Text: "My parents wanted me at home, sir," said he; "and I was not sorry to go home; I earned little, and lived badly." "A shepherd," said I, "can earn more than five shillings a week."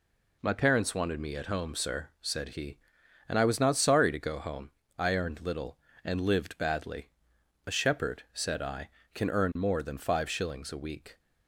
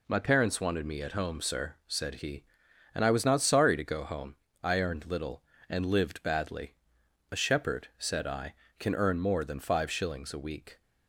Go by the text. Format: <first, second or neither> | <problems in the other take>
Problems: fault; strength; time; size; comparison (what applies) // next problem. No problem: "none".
neither | none